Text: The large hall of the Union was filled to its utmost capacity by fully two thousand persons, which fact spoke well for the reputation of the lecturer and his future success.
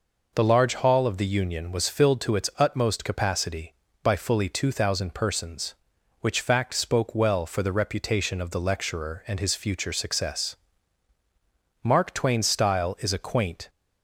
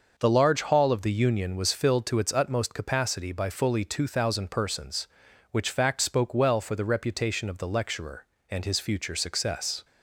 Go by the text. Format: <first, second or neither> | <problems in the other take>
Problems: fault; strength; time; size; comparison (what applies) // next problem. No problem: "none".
second | goes on to say "Mark Twain's style is a quaint"; strong; from 11.8 s on; 1.8 s long